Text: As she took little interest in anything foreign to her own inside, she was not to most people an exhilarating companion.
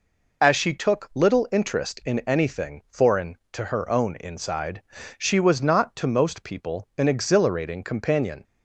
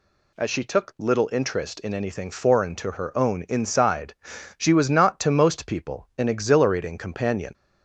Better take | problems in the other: neither | none

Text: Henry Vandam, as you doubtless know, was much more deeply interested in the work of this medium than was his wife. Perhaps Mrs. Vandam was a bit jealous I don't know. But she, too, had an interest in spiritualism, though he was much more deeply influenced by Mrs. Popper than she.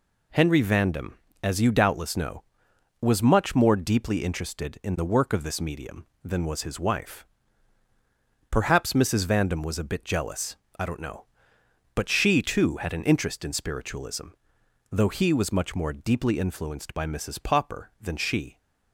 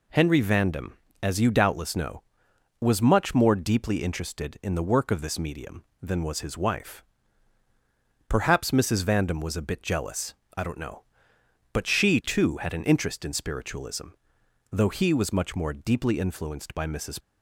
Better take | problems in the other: first | pauses between "jealous" and "I"; slight; at 10.3 s; 0.24 s long; slight in the first // stops before "Popper than she"; at 17.2 s

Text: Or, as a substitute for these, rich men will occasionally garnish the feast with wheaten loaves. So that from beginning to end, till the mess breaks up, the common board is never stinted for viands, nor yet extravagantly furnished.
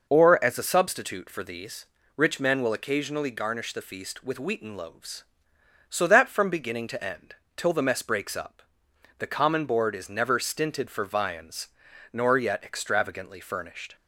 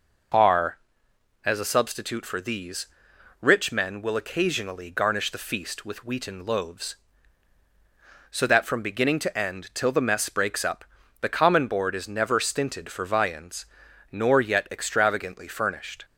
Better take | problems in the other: first | says "Are" for "Or"; at 0.3 s

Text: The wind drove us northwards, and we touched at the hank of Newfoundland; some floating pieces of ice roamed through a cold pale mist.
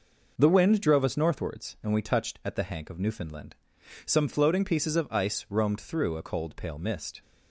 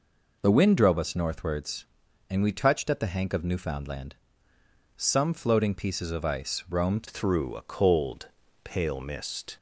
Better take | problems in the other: first | changes voice at "through"; from 7.0 s on; 2.5 s long // pauses between "cold" and "pale"; slight; at 8.2 s; 0.34 s long

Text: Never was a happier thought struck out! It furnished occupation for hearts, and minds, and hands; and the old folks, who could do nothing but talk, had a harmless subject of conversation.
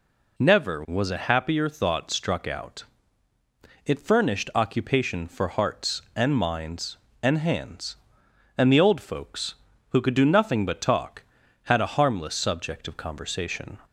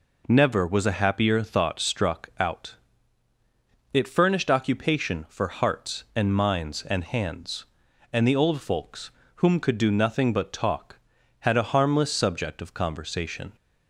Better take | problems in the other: first | says "whom" for "who"; at 9.3 s

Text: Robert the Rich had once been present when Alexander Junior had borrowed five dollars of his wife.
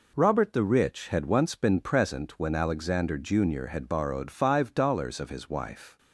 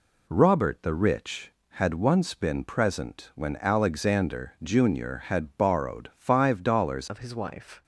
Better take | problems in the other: first | changes voice at "of"; from 7.0 s on; 0.8 s long

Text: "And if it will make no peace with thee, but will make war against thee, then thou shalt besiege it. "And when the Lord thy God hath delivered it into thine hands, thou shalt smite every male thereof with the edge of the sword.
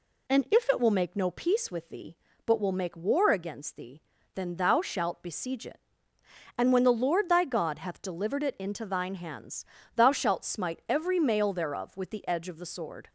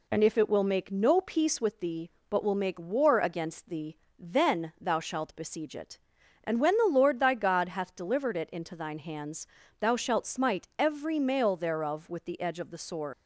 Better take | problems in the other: first | leaves "sword" unfinished; at 13.1 s; 120 ms

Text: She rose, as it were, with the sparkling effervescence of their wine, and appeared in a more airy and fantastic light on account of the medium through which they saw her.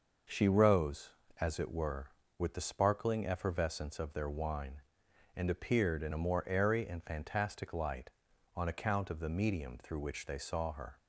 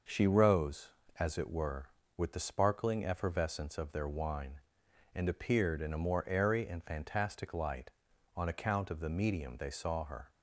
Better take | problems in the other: first | skips "through which"; at 9.5 s

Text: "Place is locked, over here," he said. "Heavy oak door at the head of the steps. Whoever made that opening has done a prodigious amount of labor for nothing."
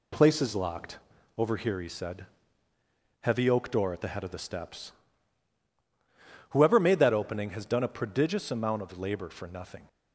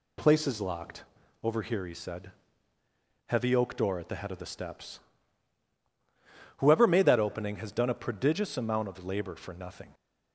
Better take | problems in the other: second | gets quieter; noticeable; throughout; 4 dB

